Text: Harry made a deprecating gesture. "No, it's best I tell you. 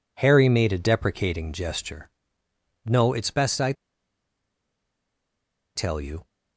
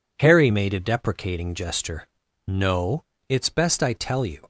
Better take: second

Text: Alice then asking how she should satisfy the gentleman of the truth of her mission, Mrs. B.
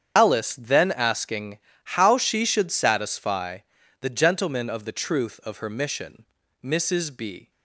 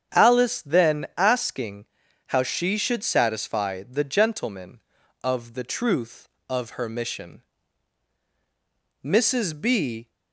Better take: second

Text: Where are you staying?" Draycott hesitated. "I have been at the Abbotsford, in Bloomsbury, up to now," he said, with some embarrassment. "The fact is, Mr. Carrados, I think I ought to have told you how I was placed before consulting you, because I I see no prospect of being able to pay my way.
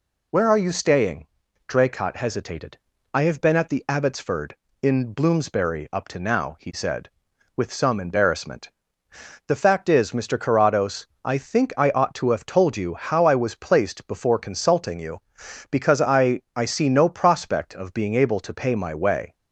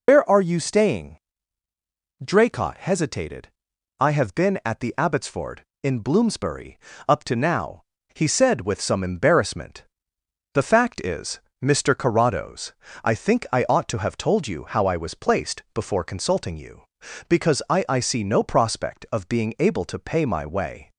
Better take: first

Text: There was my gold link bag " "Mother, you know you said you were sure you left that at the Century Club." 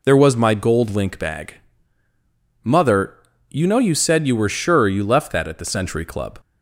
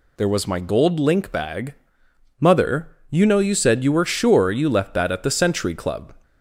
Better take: neither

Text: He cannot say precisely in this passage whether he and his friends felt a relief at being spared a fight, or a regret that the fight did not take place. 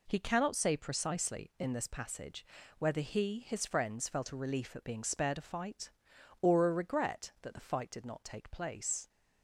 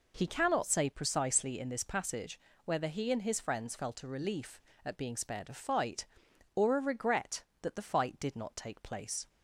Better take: second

